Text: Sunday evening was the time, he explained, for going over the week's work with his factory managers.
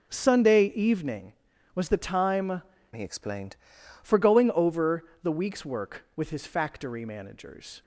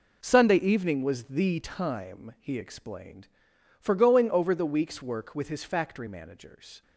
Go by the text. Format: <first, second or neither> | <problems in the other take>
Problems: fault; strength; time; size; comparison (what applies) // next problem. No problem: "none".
second | starts louder than the rest; strong; until 1.2 s; 7.5 dB // changes voice from "he" to "explained"; from 2.9 to 3.5 s; 0.6 s long // pauses between "over" and "the"; slight; at 5.0 s; 0.18 s long